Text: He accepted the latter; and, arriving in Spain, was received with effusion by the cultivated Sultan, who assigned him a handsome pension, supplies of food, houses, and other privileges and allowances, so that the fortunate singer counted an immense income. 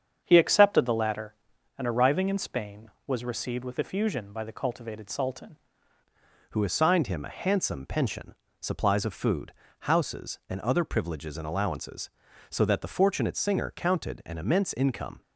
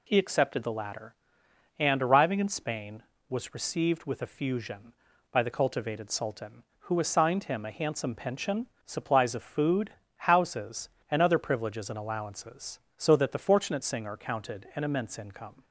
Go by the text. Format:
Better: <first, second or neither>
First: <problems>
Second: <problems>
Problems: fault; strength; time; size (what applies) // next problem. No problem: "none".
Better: second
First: starts louder than the rest; strong; until 1.2 s; 7.5 dB // changes voice at "who"; from 6.5 s on; 8.7 s long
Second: none